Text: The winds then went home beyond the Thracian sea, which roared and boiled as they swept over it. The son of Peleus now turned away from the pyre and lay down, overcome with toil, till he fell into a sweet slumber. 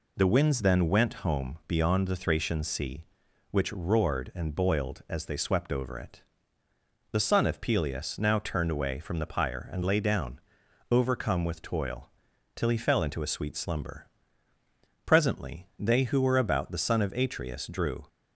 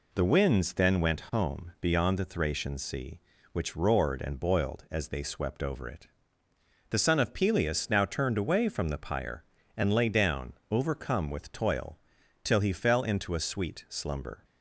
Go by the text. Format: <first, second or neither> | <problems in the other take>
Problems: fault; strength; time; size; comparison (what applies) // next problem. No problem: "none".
second | goes on to say "Presently they who were about the son of Atreus drew"; strong; from 15.0 s on; 3.0 s long